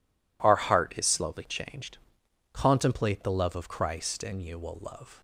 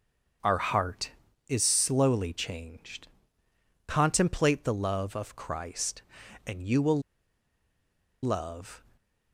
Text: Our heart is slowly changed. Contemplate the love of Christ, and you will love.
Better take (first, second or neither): first